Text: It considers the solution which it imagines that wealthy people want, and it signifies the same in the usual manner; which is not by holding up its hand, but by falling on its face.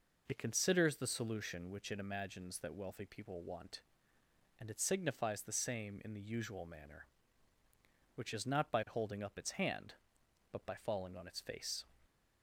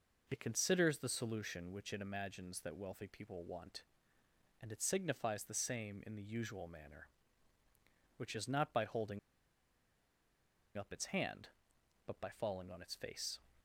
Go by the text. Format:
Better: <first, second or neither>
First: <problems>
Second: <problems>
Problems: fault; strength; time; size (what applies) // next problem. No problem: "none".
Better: first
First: none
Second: pauses between "holding" and "up"; strong; at 9.1 s; 1.5 s long